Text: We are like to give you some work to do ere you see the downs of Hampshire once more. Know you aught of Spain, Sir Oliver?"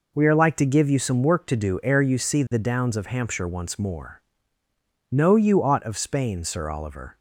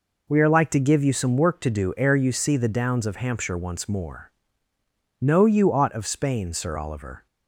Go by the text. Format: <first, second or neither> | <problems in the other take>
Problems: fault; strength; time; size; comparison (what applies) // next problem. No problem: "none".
neither | none